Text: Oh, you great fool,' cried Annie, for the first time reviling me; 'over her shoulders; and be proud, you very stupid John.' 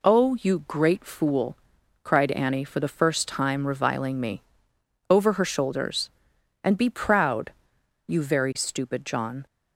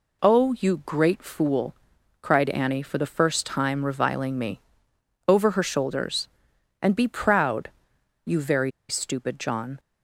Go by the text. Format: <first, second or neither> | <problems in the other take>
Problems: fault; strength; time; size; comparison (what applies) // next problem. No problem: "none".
first | pauses between "very" and "stupid"; slight; at 8.7 s; 0.18 s long